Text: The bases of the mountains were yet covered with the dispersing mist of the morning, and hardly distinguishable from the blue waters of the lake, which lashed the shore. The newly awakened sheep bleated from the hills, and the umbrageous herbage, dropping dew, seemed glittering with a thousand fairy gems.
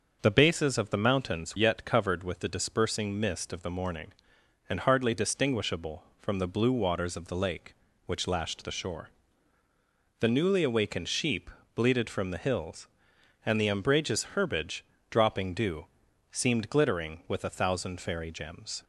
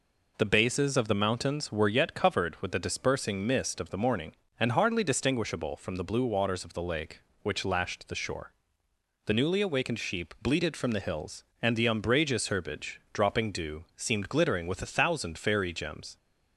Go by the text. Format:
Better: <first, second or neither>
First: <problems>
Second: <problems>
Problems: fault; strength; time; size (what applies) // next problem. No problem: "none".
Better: second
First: starts louder than the rest; until 1.2 s; 6 dB // skips "were"; at 1.5 s // pauses between "sheep" and "bleated"; slight; at 11.4 s; 0.24 s long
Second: none